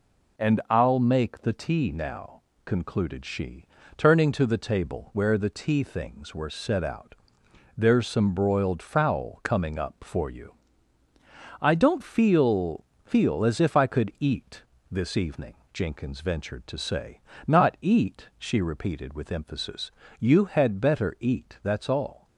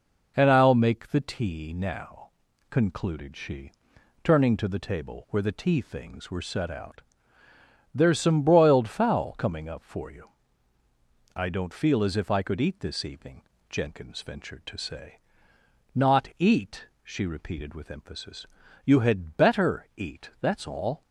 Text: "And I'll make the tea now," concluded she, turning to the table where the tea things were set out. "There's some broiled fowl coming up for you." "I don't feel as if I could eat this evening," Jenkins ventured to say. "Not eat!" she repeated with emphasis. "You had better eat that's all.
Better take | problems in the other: second | says "feel" twice; at 13.0 s // pauses between "eat" and "this"; slight; at 14.6 s; 0.26 s long

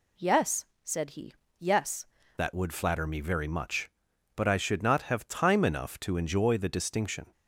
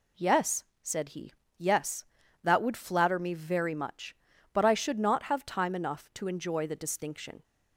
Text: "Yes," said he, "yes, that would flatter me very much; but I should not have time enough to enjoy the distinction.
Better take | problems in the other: second | changes voice at "that"; from 2.3 s on; 5.0 s long

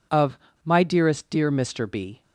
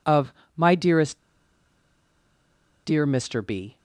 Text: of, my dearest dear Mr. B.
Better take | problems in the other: first | pauses between "dearest" and "dear"; strong; at 1.1 s; 1.6 s long

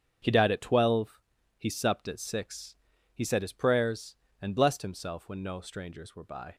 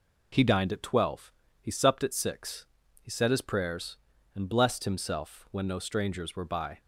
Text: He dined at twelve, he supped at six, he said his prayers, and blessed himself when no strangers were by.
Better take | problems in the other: second | starts louder than the rest; strong; until 1.6 s; 7.5 dB // says "died" for "dined"; at 0.3 s

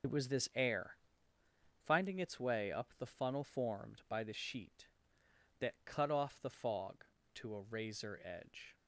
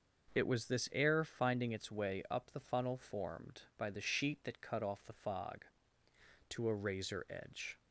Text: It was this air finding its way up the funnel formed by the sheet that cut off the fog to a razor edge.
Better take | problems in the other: second | loses the start of "It"; at 0.0 s; 50 ms // starts louder than the rest; until 1.9 s; 6.5 dB // pauses between "air" and "finding"; noticeable; at 0.9 s; 0.88 s long

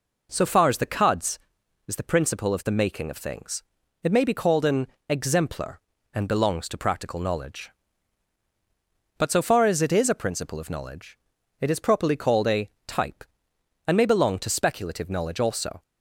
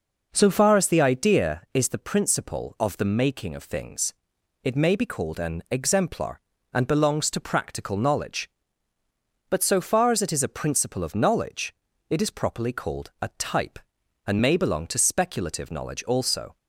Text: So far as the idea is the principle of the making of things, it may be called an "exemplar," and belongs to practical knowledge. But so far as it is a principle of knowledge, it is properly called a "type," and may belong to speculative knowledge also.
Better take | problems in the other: second | says "cuds" for "idea"; at 0.8 s // pauses between "an" and "exemplar"; slight; at 4.8 s; 0.24 s long // pauses between "a" and "type"; slight; at 12.6 s; 0.16 s long

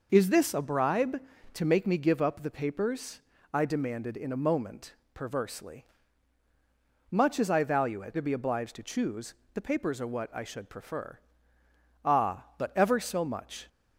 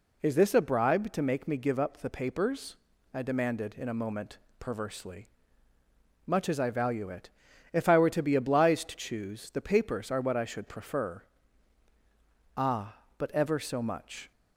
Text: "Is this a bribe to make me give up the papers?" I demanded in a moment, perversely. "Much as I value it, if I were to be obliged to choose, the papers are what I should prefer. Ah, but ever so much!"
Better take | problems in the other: second | skips "if I were"; at 8.1 s

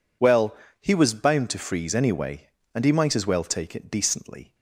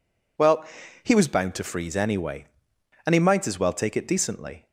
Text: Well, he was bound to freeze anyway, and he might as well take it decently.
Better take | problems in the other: neither | none

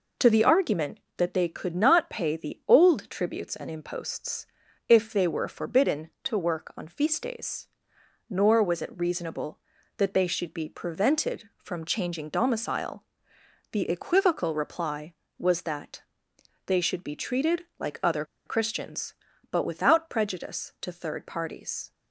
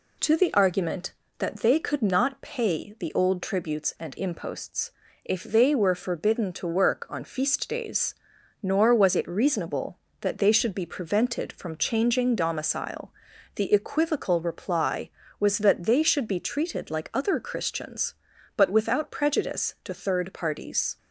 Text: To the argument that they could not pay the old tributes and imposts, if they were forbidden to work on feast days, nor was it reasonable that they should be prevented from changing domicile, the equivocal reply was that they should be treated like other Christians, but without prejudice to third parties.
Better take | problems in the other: second | pauses between "that" and "they"; noticeable; at 16.0 s; 0.64 s long // pauses between "other" and "Christians"; slight; at 18.2 s; 0.22 s long

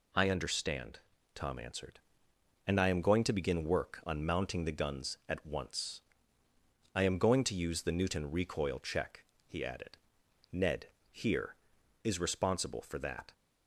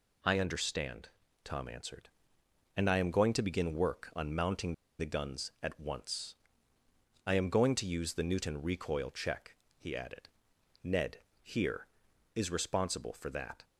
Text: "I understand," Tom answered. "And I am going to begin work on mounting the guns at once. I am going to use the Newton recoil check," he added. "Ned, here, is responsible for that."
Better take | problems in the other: first | pauses between "mounting" and "the"; slight; at 4.7 s; 0.25 s long

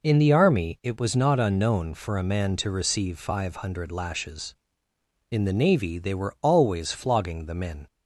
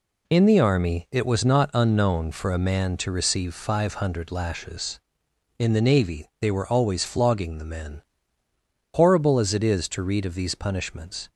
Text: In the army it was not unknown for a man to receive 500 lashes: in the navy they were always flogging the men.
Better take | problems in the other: first | goes on to say "Horrible as it is to read of these punishments"; strong; from 8.9 s on; 2.3 s long

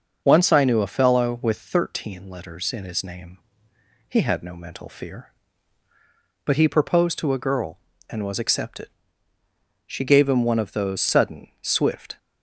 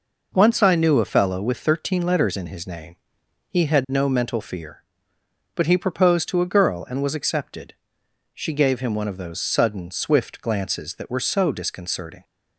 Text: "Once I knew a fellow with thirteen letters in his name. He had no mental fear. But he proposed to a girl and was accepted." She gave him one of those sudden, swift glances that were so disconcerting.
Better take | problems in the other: second | starts louder than the rest; noticeable; until 1.2 s; 6 dB // stops before "glances that were so disconcerting"; at 12.1 s

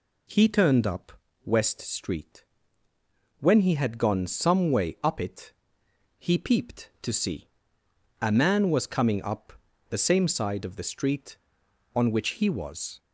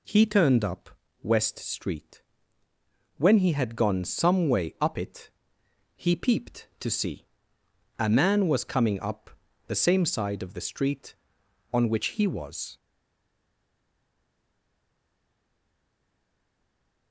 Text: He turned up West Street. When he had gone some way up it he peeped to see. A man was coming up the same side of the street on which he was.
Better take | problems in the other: first | pauses between "up" and "West"; slight; at 0.9 s; 0.32 s long; slight in the first // pauses between "it" and "he"; noticeable; at 5.3 s; 0.64 s long; noticeable in the first // pauses between "up" and "the"; slight; at 9.3 s; 0.36 s long; slight in the first // stays silent after the last word; strong; from 12.7 s on; 4.4 s long

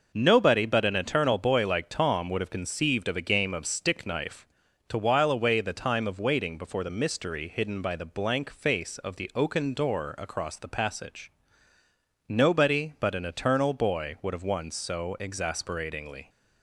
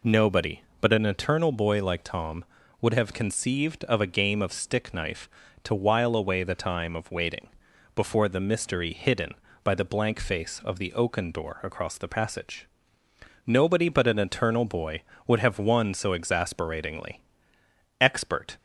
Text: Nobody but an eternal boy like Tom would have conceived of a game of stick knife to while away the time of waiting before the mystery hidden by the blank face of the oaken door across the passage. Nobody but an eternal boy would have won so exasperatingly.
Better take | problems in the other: first | pauses between "waiting" and "before"; noticeable; at 7.4 s; 0.48 s long // goes on to say "Expert"; from 17.9 s on; 0.58 s long

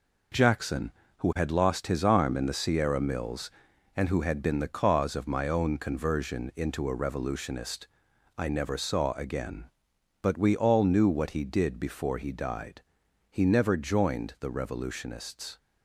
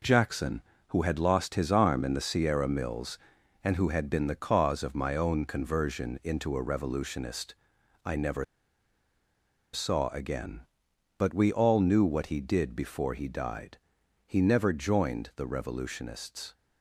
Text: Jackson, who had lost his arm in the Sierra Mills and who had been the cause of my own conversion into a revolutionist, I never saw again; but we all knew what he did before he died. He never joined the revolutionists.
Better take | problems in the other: first | pauses between "never" and "saw"; strong; at 8.4 s; 1.3 s long

